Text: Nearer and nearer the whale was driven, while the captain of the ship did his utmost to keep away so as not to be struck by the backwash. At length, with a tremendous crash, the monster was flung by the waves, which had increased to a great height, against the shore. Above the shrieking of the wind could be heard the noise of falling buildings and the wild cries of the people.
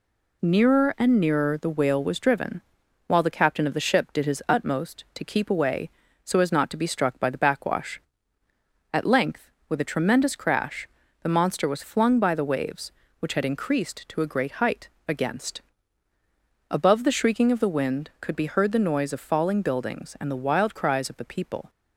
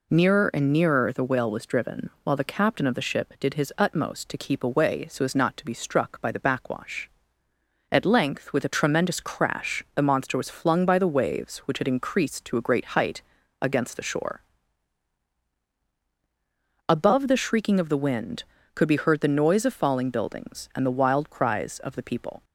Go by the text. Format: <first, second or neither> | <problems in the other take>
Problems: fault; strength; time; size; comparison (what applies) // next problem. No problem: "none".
second | skips "the shore"; at 16.1 s